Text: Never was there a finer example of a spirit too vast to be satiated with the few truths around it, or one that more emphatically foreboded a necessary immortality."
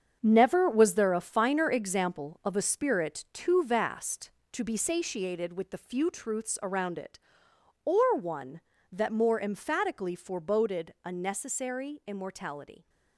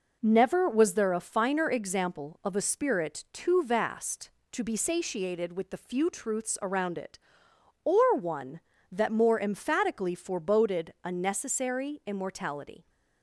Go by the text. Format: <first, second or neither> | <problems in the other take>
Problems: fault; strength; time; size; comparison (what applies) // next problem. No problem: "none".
second | gets quieter; strong; throughout; 9 dB